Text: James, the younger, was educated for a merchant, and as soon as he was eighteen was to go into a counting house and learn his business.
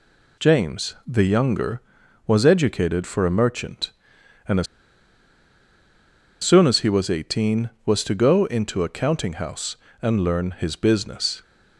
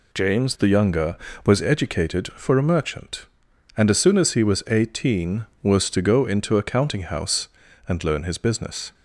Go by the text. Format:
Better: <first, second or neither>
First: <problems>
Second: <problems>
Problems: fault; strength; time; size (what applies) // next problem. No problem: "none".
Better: second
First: pauses between "as" and "soon"; strong; at 4.6 s; 1.7 s long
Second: none